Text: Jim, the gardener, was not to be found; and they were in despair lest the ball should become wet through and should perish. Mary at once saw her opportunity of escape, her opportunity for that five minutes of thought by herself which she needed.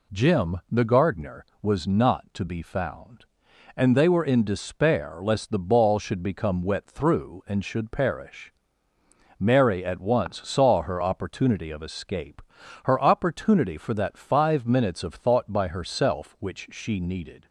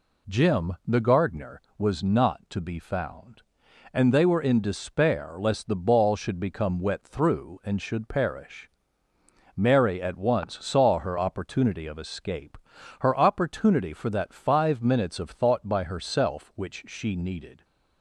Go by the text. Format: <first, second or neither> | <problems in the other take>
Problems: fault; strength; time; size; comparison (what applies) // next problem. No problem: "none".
neither | none